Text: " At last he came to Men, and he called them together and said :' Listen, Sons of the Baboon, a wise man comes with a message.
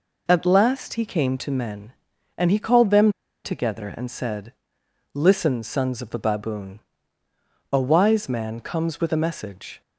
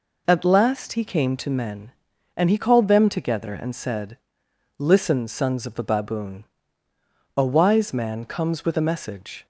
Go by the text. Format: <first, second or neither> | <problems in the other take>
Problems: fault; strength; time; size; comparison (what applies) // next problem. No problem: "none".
second | pauses between "them" and "together"; slight; at 3.1 s; 0.32 s long